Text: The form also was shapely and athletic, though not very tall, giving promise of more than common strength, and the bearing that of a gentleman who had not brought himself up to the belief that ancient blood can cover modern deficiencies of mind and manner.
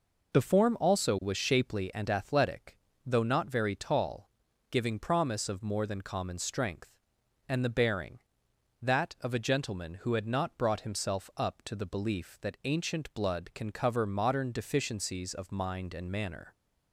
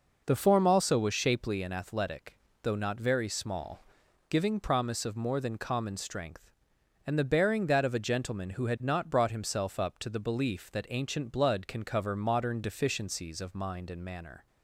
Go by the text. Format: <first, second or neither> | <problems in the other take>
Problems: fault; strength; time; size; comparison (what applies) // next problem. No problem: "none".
first | says "small" for "tall"; at 3.2 s